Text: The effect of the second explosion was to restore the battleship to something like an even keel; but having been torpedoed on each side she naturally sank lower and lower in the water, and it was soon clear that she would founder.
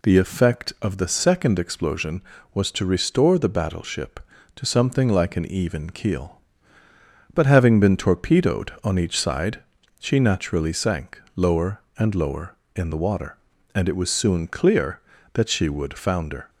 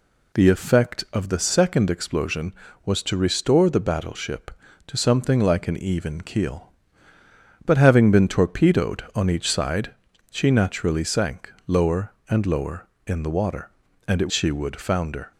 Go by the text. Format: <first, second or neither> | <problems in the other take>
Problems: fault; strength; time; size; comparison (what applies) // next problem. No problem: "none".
first | pauses between "side" and "she"; at 9.9 s; 0.38 s long; also in the first // skips "was soon clear that"; at 14.3 s